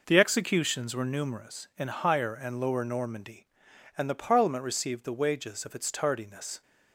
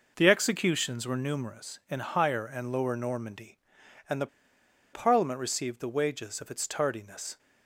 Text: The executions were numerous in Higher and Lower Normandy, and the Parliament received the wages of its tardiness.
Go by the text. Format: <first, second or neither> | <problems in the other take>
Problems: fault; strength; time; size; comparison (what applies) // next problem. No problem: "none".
first | pauses between "the" and "Parliament"; noticeable; at 4.2 s; 0.67 s long